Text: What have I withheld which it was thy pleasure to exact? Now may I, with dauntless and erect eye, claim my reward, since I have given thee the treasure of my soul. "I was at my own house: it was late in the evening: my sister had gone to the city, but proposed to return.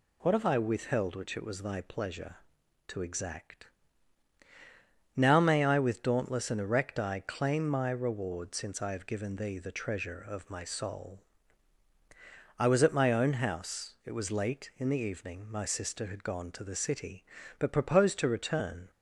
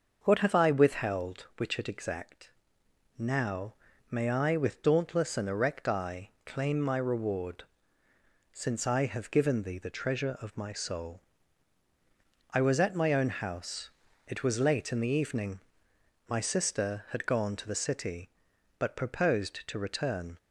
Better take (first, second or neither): first